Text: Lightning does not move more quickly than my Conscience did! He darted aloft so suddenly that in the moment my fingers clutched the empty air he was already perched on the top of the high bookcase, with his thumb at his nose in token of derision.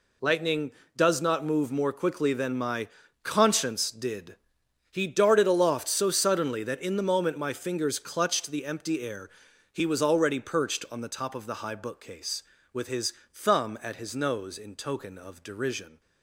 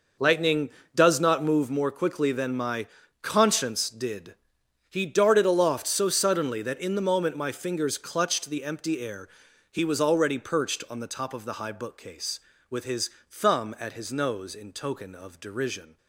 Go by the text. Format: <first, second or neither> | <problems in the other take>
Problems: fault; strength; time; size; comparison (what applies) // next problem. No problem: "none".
first | starts louder than the rest; noticeable; until 1.7 s; 5.5 dB // pauses between "my" and "Conscience"; slight; at 2.8 s; 0.34 s long; slight in the first // pauses between "air" and "he"; noticeable; at 9.2 s; 0.46 s long; noticeable in the first // pauses between "his" and "thumb"; slight; at 13.0 s; 0.22 s long; slight in the first